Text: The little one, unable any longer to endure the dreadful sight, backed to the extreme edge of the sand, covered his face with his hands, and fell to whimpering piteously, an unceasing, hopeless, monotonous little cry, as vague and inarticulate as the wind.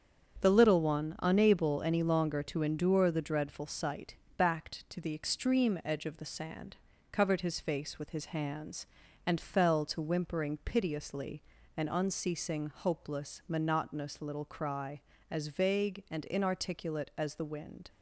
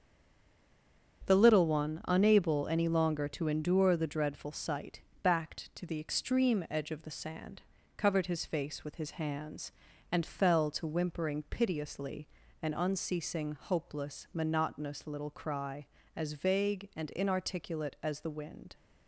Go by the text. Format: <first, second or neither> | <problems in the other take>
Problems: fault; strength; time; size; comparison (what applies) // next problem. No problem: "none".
first | stays silent before the first word; noticeable; until 1.2 s; 1.2 s long // starts louder than the rest; strong; until 2.3 s; 8 dB; strong in the first